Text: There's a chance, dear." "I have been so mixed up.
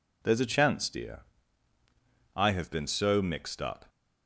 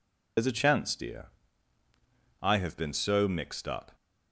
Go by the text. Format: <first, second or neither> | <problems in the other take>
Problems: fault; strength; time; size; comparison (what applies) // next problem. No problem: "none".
first | loses the start of "There's"; at 0.3 s; 75 ms